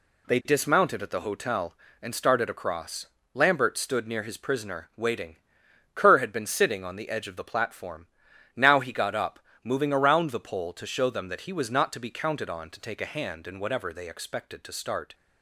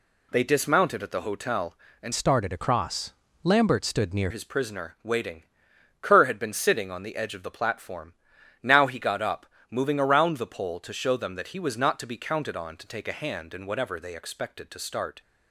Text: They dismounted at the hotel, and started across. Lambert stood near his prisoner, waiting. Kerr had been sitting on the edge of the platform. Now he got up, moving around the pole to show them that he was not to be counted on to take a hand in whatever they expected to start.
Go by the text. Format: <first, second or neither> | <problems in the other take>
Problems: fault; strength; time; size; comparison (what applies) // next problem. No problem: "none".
first | changes voice from "started" to "near"; from 2.1 to 4.2 s; 2.1 s long